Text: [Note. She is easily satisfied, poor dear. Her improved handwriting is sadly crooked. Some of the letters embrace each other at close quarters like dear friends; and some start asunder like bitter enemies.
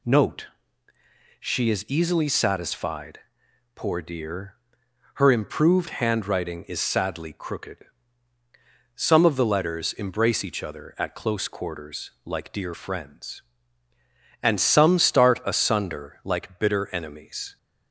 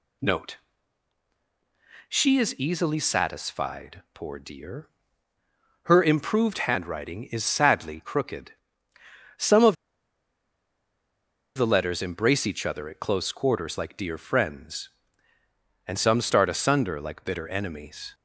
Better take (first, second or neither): first